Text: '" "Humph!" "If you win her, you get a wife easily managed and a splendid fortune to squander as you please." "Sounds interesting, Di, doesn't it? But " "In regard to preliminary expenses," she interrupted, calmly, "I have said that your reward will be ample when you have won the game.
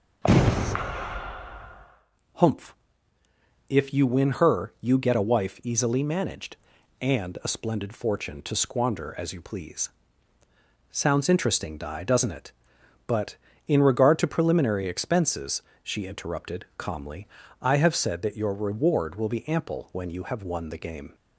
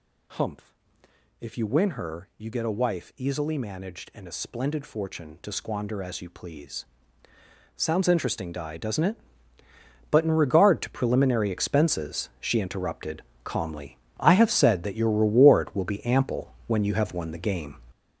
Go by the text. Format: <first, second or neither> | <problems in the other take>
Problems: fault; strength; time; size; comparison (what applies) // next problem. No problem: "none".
first | gets louder; strong; throughout; 8.5 dB